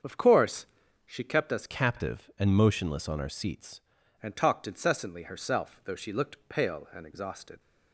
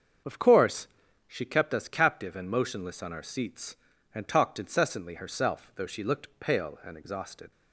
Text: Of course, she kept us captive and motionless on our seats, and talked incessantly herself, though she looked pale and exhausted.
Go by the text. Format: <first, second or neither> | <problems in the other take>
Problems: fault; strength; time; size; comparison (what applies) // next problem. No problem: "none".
second | starts louder than the rest; until 1.4 s; 7 dB; also in the second // changes voice from "captive" to "seats"; from 1.6 to 3.8 s; 2.2 s long